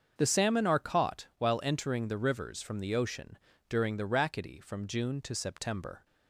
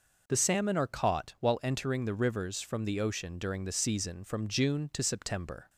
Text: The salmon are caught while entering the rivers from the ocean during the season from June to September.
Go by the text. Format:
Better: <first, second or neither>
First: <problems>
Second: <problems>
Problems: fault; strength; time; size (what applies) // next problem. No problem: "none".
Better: second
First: starts louder than the rest; until 1.1 s; 7 dB // pauses between "ocean" and "during"; slight; at 3.3 s; 0.32 s long // says "rackety" for "season"; at 4.0 s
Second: none